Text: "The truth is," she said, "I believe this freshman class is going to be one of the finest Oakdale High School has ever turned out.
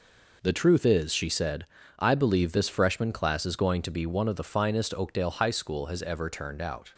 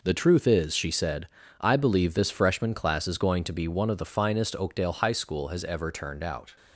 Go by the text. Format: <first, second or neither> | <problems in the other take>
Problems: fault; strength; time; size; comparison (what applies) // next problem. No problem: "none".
neither | none